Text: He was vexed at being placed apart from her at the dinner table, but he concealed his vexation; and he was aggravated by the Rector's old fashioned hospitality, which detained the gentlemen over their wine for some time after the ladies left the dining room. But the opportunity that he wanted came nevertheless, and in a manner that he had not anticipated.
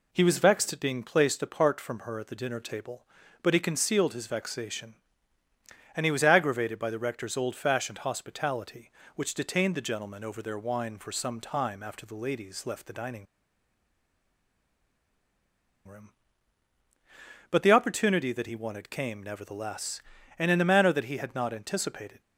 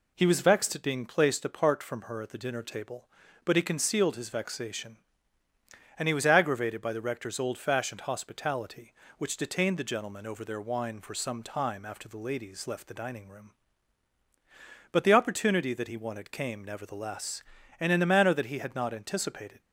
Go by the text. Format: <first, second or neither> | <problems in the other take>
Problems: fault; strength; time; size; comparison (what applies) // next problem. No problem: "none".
second | pauses between "dining" and "room"; strong; at 13.2 s; 2.6 s long